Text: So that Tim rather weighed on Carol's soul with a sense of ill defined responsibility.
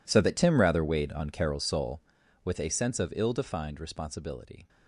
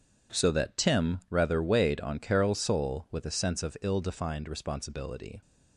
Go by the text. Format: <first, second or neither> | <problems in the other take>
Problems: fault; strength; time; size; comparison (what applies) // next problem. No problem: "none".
second | gets quieter; strong; throughout; 19 dB